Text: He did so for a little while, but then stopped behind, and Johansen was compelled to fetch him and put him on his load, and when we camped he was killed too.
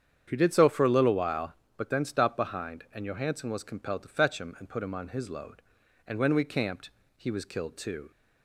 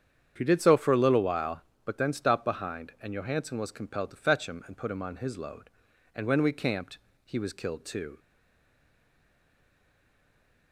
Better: first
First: starts louder than the rest; strong; until 1.2 s; 8.5 dB // pauses between "camped" and "he"; slight; at 6.9 s; 0.26 s long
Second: starts louder than the rest; strong; until 1.3 s; 8.5 dB // pauses between "camped" and "he"; slight; at 6.9 s; 0.26 s long // stays silent after the last word; strong; from 8.1 s on; 2.6 s long

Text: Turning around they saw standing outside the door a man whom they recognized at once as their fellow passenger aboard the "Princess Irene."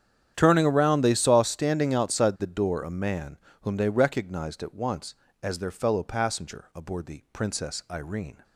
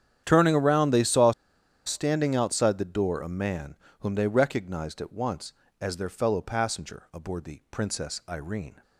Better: first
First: starts louder than the rest; strong; until 1.3 s; 9.5 dB // pauses between "man" and "whom"; slight; at 3.3 s; 0.26 s long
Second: starts louder than the rest; strong; until 1.2 s; 9.5 dB // pauses between "saw" and "standing"; noticeable; at 1.3 s; 0.55 s long // pauses between "man" and "whom"; slight; at 3.7 s; 0.26 s long

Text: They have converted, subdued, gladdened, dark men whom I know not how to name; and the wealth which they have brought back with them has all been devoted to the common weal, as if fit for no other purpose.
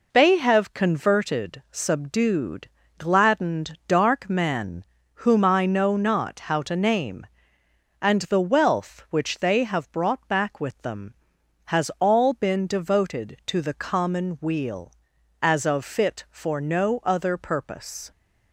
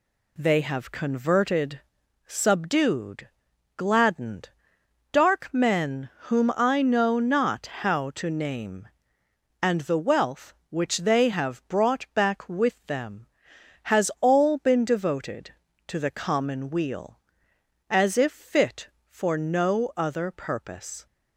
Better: second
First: pauses between "men" and "whom"; slight; at 4.8 s; 0.32 s long // says "of" for "if"; at 15.6 s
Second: none

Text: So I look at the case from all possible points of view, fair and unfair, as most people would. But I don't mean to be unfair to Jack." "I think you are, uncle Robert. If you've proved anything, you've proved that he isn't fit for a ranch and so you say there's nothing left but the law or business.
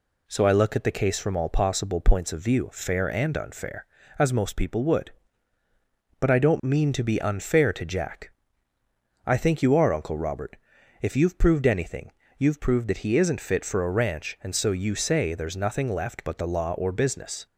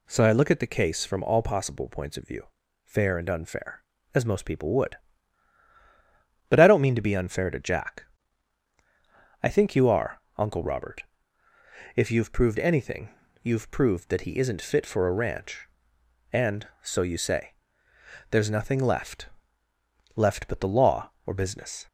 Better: first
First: none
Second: pauses between "say" and "there's"; noticeable; at 17.5 s; 0.78 s long // says "left" twice; at 20.1 s

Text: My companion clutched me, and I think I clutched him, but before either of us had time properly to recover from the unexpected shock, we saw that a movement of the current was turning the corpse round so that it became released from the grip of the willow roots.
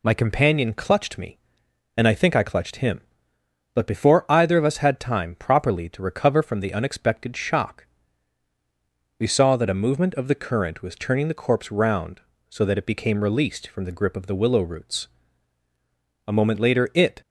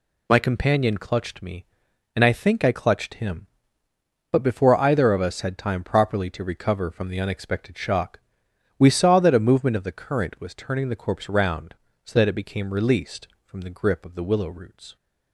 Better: second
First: goes on to say "A moment later it"; noticeable; from 16.2 s on; 0.94 s long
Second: none

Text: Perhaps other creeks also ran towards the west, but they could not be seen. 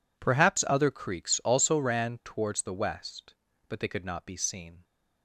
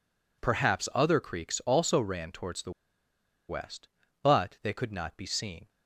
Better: first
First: none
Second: pauses between "the" and "west"; noticeable; at 2.6 s; 0.78 s long

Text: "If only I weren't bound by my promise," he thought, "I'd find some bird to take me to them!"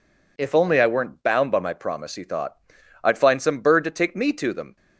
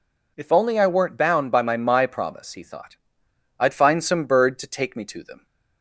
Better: first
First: none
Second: says "my" twice; at 1.7 s

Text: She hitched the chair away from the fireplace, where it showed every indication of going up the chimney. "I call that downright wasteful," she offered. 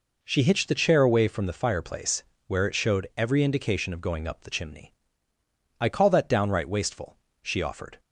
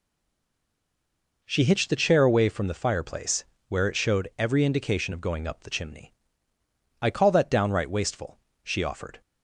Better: first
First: none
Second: stays silent before the first word; noticeable; until 1.4 s; 1.4 s long

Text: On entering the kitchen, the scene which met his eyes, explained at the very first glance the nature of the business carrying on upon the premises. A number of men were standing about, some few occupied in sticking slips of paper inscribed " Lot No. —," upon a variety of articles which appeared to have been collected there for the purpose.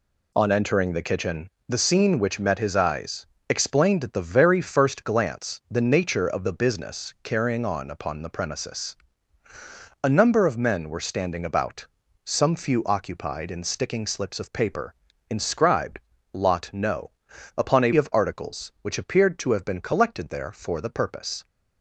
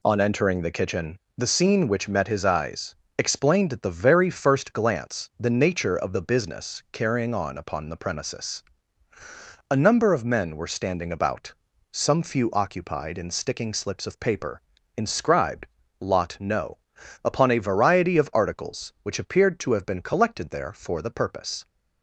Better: second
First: pauses between "paper" and "inscribed"; slight; at 14.9 s; 0.34 s long // skips "variety"; at 17.9 s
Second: pauses between "paper" and "inscribed"; slight; at 14.6 s; 0.34 s long

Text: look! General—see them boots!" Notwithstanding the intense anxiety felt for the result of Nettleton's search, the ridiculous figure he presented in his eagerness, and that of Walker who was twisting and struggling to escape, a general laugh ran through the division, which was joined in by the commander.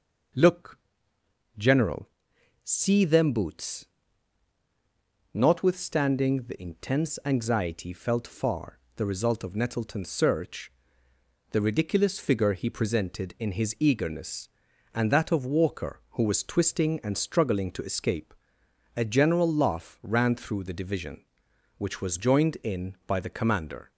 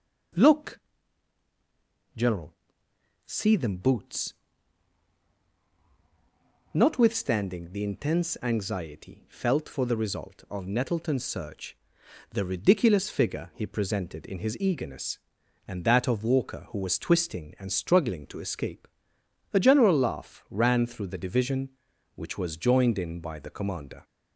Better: second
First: says "far" for "for"; at 8.2 s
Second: none

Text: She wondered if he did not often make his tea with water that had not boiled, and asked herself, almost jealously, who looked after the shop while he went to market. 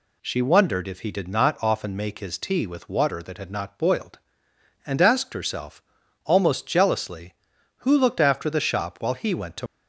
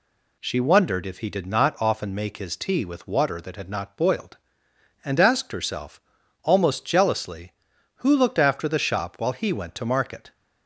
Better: second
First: stops before "market"; at 9.6 s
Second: none

